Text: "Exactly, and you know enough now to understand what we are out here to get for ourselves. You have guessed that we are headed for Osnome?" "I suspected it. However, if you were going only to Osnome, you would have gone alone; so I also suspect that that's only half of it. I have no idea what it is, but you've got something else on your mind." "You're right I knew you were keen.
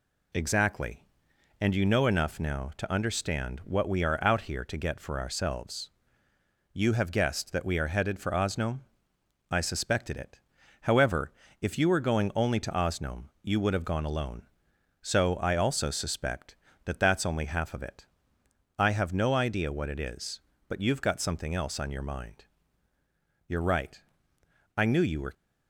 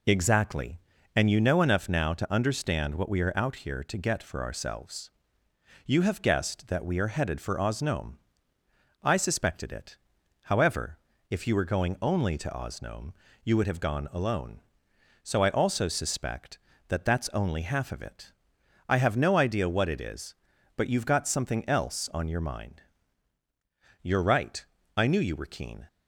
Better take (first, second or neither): second